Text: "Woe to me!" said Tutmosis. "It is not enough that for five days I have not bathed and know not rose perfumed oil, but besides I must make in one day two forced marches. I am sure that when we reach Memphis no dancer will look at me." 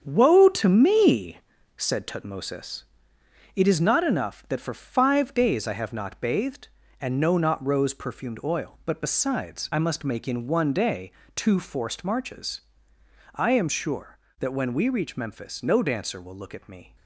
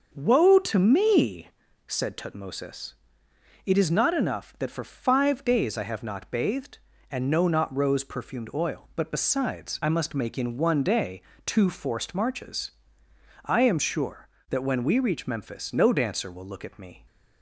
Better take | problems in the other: second | gets quieter; strong; throughout; 8 dB // starts louder than the rest; strong; until 1.0 s; 7.5 dB; also in the second // pauses between "day" and "two"; slight; at 11.1 s; 0.24 s long; slight in the second

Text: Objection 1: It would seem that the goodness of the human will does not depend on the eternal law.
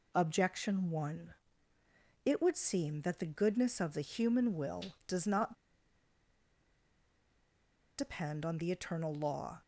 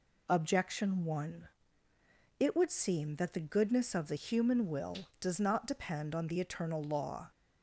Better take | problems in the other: second | pauses between "not" and "depend"; strong; at 5.5 s; 2.4 s long

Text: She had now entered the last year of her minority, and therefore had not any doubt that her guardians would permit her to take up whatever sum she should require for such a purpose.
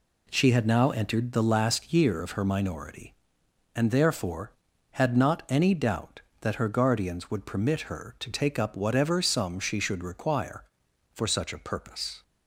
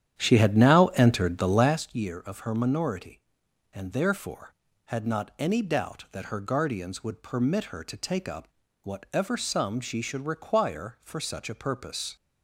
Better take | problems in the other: first | starts louder than the rest; strong; until 1.8 s; 10 dB // pauses between "up" and "whatever"; slight; at 8.4 s; 0.36 s long

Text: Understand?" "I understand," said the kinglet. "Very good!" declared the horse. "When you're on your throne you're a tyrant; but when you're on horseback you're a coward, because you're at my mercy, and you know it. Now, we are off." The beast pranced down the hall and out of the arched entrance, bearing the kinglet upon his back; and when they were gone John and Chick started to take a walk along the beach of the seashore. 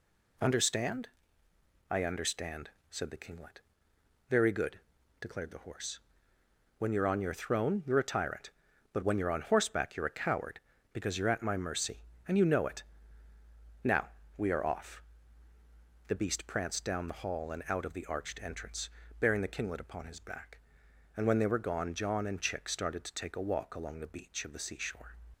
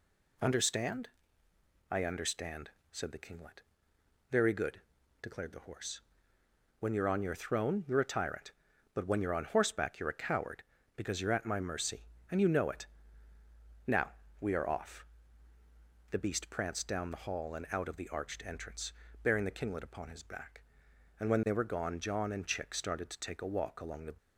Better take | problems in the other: first | stops before "beach of the seashore"; at 24.1 s

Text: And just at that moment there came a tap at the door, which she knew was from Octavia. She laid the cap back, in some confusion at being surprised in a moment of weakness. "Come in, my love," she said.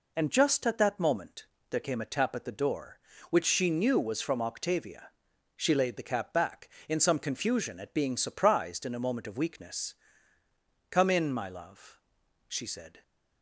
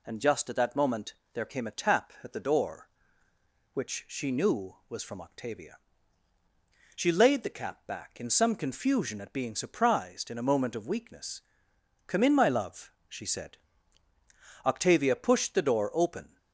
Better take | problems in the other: first | pauses between "moment" and "there"; slight; at 1.1 s; 0.20 s long; slight in the first // goes on to say "Octavia pushed the door open"; strong; from 14.6 s on; 1.7 s long

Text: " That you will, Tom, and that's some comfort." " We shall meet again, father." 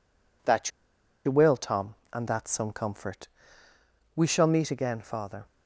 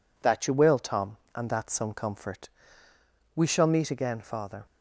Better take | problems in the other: second | pauses between "That" and "you"; noticeable; at 0.7 s; 0.55 s long

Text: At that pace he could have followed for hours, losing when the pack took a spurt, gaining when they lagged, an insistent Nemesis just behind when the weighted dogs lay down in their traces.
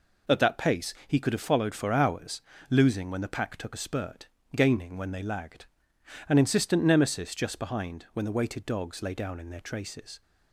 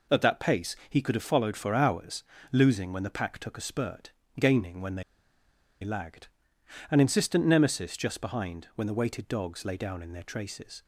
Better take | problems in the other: first | pauses between "they" and "lagged"; noticeable; at 5.0 s; 0.80 s long

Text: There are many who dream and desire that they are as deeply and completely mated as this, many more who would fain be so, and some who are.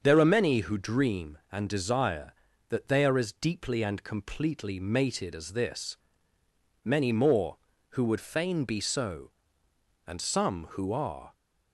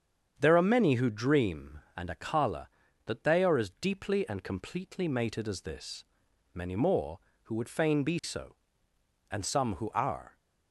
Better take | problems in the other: first | starts louder than the rest; strong; until 1.3 s; 7.5 dB; also in the first // says "akala" for "desire"; at 2.0 s

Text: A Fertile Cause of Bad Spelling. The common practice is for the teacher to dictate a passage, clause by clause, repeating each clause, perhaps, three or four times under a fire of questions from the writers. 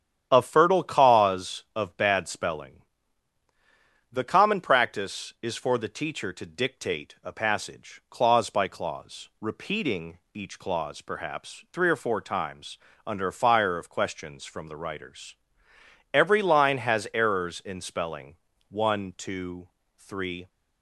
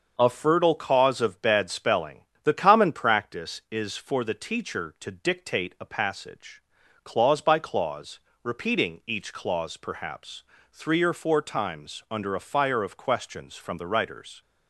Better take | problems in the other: second | starts louder than the rest; strong; until 1.3 s; 9.5 dB; also in the second // pauses between "repeating" and "each"; slight; at 10.1 s; 0.16 s long // pauses between "times" and "under"; slight; at 12.7 s; 0.30 s long // goes on to say "Every line has errors in spelling one two three"; strong; from 16.1 s on; 4.3 s long

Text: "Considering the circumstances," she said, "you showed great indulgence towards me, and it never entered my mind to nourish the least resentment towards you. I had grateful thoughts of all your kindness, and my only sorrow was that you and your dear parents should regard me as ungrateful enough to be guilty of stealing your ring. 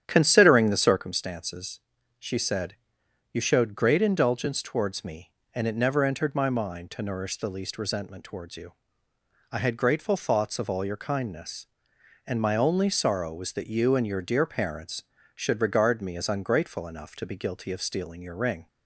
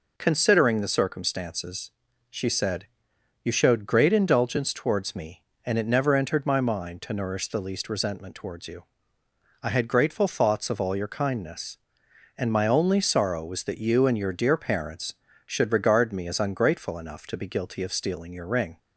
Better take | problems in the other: second | starts louder than the rest; strong; until 1.2 s; 9.5 dB

